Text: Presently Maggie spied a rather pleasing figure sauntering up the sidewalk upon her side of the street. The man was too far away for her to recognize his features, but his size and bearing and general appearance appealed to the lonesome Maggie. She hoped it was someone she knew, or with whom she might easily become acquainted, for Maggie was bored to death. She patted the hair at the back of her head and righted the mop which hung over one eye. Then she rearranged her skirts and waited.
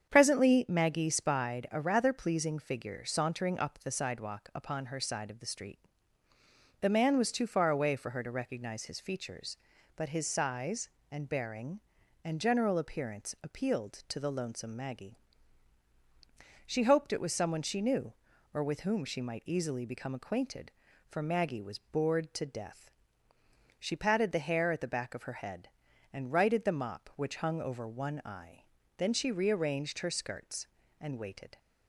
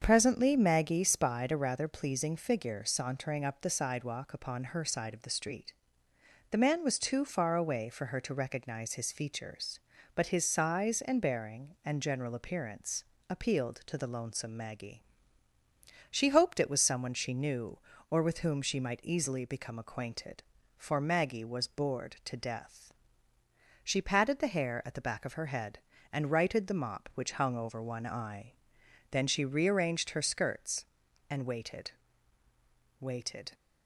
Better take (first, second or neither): first